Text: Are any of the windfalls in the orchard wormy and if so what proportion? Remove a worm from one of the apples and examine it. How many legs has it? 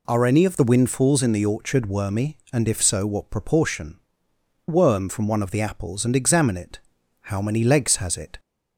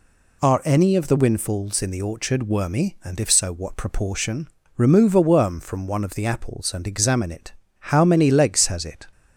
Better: second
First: skips "Remove a"; at 4.3 s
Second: none

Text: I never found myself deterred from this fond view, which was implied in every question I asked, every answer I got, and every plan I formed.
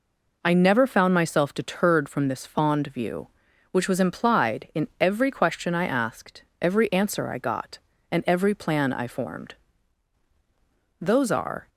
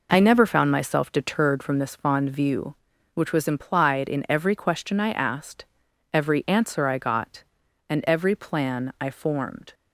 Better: second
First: goes on to say "Those are"; noticeable; from 11.0 s on; 0.68 s long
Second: none

